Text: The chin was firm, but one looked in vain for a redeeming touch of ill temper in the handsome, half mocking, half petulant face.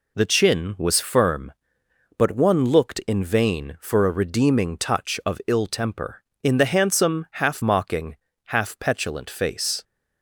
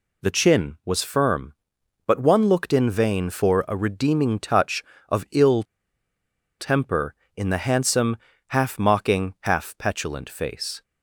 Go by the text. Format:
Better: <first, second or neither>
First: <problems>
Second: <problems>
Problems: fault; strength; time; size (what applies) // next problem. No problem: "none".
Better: first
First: none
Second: pauses between "ill" and "temper"; noticeable; at 5.6 s; 0.96 s long